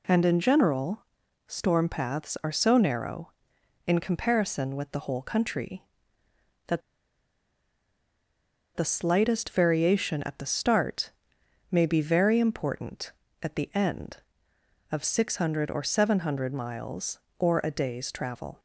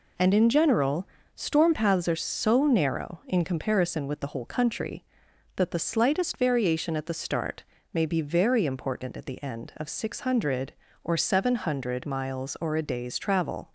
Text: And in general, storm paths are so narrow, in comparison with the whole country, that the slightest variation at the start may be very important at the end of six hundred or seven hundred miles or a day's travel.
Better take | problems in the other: second | pauses between "that" and "the"; strong; at 6.8 s; 1.9 s long // pauses between "start" and "may"; noticeable; at 11.1 s; 0.60 s long; slight in the second

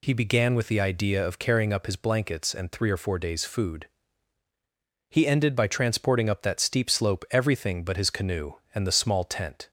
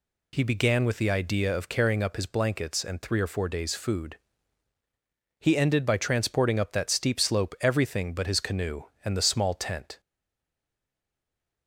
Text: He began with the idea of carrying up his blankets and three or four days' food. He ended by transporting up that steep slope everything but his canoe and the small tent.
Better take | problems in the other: first | stays silent after the last word; noticeable; from 9.9 s on; 1.7 s long

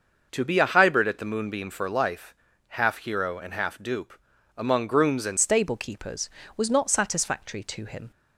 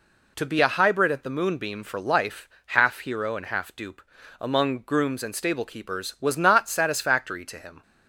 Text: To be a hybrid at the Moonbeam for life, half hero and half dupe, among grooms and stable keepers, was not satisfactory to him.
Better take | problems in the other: second | starts louder than the rest; until 1.3 s; 6 dB // changes voice at "stable"; from 5.3 s on; 2.8 s long

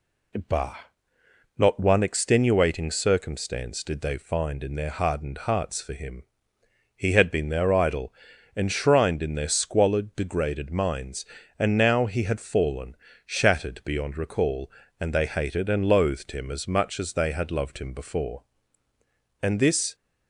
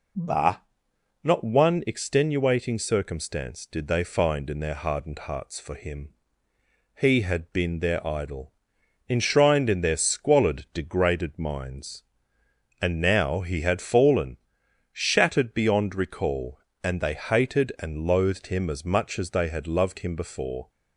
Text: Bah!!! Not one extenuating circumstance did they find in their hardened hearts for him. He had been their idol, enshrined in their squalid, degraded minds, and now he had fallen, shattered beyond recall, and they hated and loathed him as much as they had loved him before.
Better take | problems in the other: second | goes on to say "And this"; from 19.4 s on; 0.54 s long

